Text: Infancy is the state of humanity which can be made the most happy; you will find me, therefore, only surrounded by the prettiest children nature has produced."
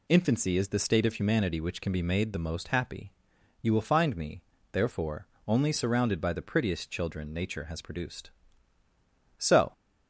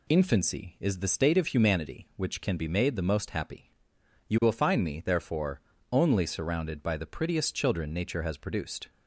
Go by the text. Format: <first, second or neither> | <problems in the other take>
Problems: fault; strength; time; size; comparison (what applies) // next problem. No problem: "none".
second | goes on to say "So"; slight; from 9.3 s on; 0.36 s long